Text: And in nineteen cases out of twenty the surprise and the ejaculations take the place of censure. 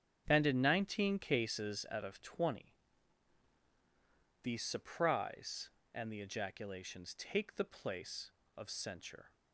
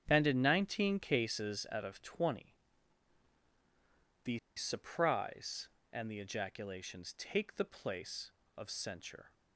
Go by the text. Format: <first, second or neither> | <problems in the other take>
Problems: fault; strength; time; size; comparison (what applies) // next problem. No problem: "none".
first | starts louder than the rest; strong; until 1.0 s; 8 dB; strong in the first // pauses between "twenty" and "the"; strong; at 2.5 s; 1.7 s long; strong in the first // pauses between "the" and "surprise"; slight; at 4.3 s; 0.18 s long